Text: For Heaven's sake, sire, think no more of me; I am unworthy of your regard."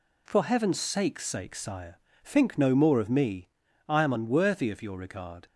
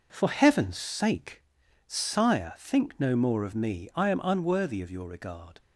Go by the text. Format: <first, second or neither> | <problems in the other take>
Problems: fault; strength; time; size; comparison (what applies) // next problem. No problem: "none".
second | says "sake" twice; at 1.2 s